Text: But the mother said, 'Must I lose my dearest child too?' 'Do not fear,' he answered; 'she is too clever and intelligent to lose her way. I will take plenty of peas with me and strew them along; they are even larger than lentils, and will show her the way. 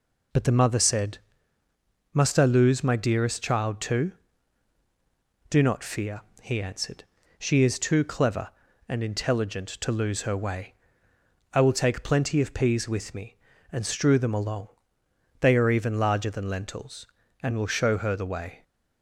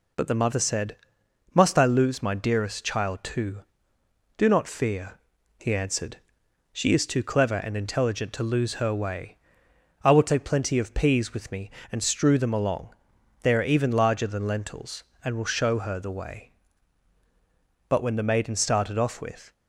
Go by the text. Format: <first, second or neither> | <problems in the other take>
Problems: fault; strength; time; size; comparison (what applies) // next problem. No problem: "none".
first | goes on to say "But when the maiden started off with"; from 17.8 s on; 1.6 s long